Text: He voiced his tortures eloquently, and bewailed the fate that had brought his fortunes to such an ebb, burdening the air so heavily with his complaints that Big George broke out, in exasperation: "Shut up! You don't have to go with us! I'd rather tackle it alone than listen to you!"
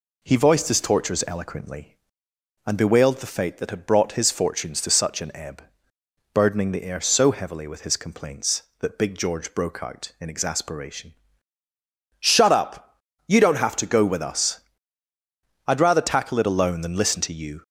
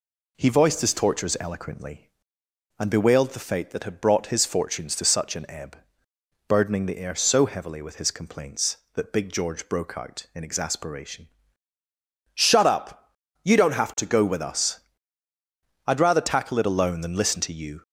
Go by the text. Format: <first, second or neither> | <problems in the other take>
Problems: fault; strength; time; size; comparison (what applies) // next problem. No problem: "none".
neither | none